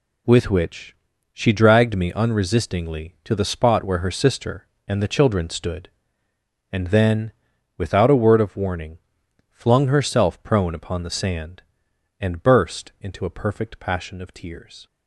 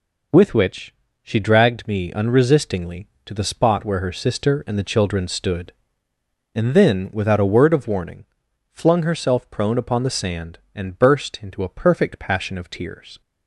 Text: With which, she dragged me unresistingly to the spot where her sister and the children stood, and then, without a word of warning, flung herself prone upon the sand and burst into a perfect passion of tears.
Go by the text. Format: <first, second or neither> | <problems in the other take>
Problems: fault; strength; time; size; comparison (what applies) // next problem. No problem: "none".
neither | none